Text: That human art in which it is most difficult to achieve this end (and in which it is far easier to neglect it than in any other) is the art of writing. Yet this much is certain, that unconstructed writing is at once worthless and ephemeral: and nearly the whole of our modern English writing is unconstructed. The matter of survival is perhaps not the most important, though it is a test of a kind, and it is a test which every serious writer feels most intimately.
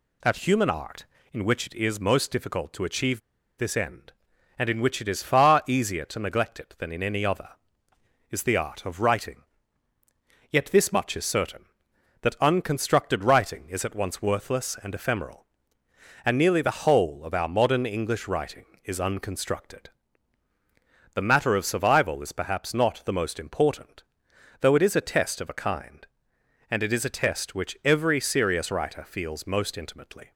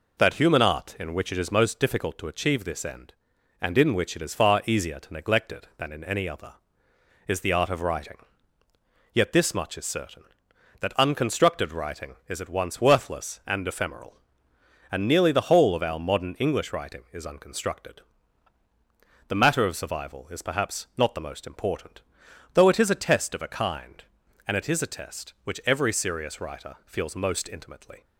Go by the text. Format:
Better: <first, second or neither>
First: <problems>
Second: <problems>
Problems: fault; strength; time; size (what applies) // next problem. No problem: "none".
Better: second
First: pauses between "achieve" and "this"; at 3.2 s; 0.37 s long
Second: none